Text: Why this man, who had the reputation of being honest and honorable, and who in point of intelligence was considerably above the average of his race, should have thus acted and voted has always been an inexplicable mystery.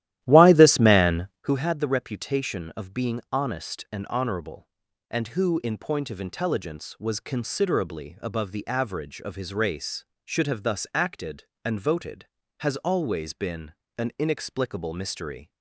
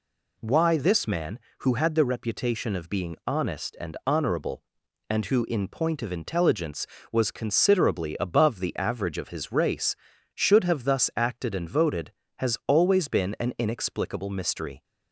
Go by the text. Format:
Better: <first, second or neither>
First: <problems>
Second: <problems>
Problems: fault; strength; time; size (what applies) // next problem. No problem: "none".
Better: second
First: starts louder than the rest; strong; until 1.6 s; 13.5 dB // pauses between "been" and "an"; slight; at 13.7 s; 0.26 s long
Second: none